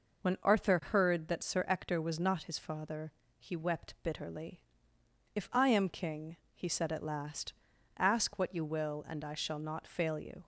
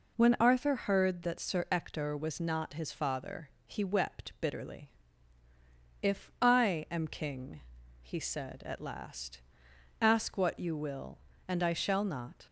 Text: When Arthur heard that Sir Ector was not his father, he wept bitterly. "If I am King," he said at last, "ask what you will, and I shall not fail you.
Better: first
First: none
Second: stops before "fail you"; at 12.4 s

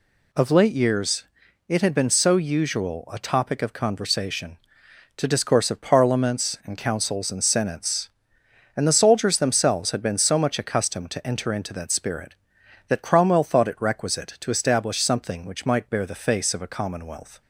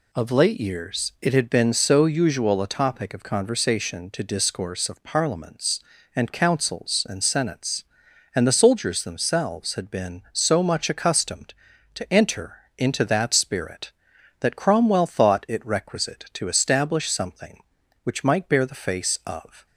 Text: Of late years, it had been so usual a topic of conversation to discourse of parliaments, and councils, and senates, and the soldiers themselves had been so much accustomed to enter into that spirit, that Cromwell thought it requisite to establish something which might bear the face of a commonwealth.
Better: first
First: none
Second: pauses between "enter" and "into"; slight; at 12.5 s; 0.22 s long // stops before "a commonwealth"; at 19.6 s

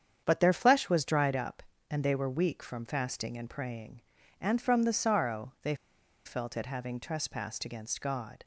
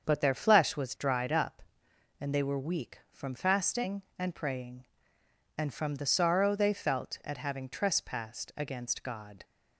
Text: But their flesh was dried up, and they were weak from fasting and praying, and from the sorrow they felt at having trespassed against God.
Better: second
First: starts louder than the rest; strong; until 1.2 s; 8 dB // pauses between "they" and "felt"; noticeable; at 5.7 s; 0.50 s long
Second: starts louder than the rest; until 1.1 s; 7 dB

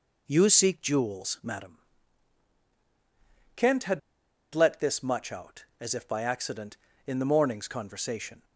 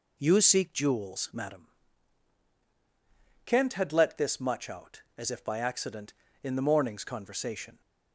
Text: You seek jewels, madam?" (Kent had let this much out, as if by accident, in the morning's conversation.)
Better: second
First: pauses between "had" and "let"; noticeable; at 3.9 s; 0.53 s long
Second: none

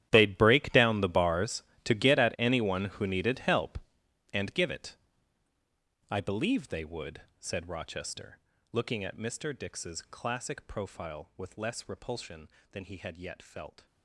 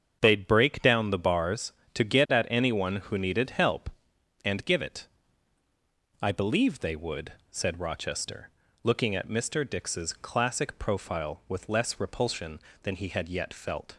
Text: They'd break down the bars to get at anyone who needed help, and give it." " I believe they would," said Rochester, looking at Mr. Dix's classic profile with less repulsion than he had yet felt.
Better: second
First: gets quieter; strong; throughout; 17 dB // starts louder than the rest; strong; until 1.1 s; 12 dB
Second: starts louder than the rest; strong; until 1.2 s; 8 dB

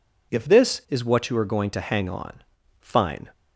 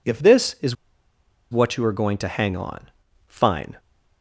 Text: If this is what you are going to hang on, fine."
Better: first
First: none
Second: pauses between "is" and "what"; noticeable; at 0.7 s; 0.75 s long

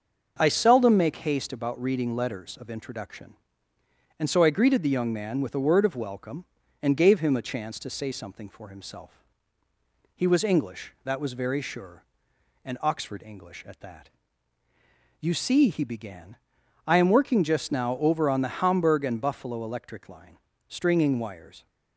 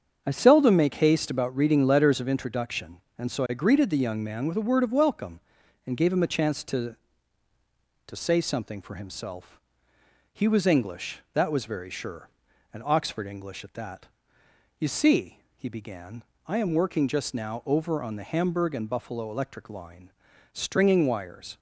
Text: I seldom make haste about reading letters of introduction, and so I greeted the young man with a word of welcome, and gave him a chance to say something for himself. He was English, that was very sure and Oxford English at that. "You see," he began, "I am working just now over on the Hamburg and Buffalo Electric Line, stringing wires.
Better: first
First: starts louder than the rest; until 1.4 s; 6.5 dB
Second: starts louder than the rest; strong; until 1.2 s; 7.5 dB // says "to" twice; at 8.0 s

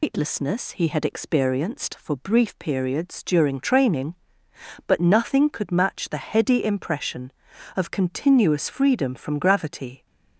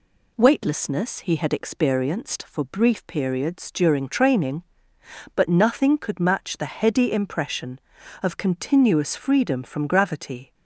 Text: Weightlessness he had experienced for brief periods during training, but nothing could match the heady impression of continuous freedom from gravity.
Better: second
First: loses the start of "Weightlessness"; at 0.0 s; 155 ms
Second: none

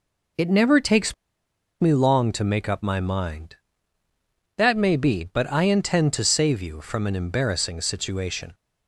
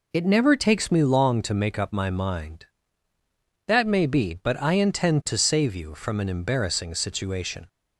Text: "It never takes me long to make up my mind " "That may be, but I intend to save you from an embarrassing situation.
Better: second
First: pauses between "takes" and "me"; noticeable; at 1.1 s; 0.67 s long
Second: none

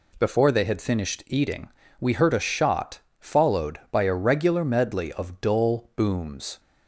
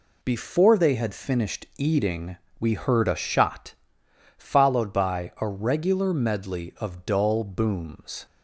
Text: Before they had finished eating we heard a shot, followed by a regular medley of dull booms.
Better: neither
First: pauses between "eating" and "we"; slight; at 1.6 s; 0.30 s long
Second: pauses between "eating" and "we"; slight; at 2.3 s; 0.24 s long

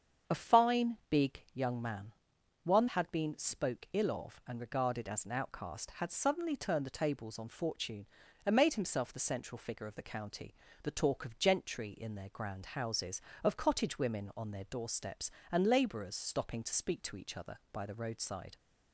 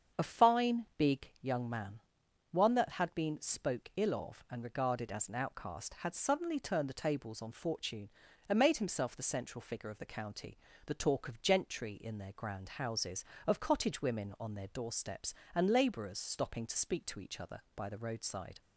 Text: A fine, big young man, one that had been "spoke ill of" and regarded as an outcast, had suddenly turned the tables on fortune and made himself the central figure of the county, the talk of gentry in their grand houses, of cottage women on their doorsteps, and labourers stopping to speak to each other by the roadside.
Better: second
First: starts louder than the rest; strong; until 1.4 s; 7.5 dB // skips "that"; at 2.8 s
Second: starts louder than the rest; strong; until 1.3 s; 7 dB

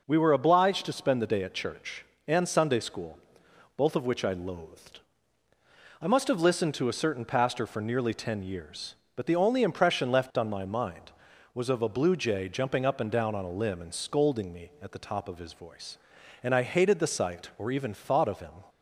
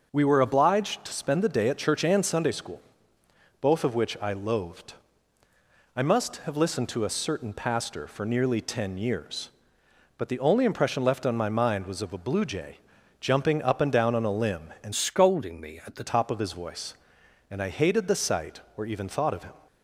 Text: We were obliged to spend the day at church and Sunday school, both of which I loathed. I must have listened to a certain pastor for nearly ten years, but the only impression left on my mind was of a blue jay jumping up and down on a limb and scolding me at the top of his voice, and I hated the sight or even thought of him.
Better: first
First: none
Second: starts louder than the rest; until 1.1 s; 6 dB // pauses between "jay" and "jumping"; at 12.7 s; 0.42 s long // changes voice from "scolding" to "the"; from 14.9 to 16.0 s; 1.1 s long

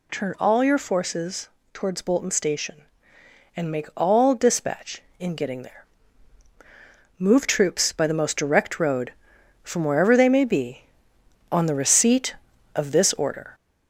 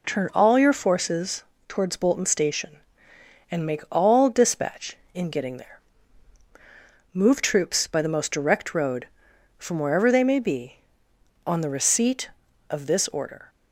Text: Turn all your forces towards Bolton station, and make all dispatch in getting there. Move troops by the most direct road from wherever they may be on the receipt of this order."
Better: second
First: gets louder; slight; throughout; 3 dB // pauses between "forces" and "towards"; slight; at 1.4 s; 0.24 s long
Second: pauses between "forces" and "towards"; slight; at 1.4 s; 0.24 s long

